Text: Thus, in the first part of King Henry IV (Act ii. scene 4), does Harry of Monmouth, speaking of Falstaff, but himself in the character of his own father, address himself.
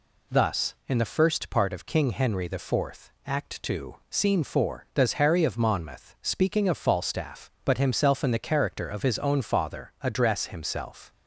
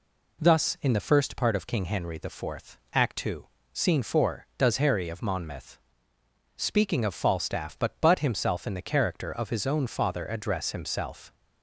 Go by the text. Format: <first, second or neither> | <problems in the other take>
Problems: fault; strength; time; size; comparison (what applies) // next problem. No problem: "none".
first | says "but" twice; at 7.9 s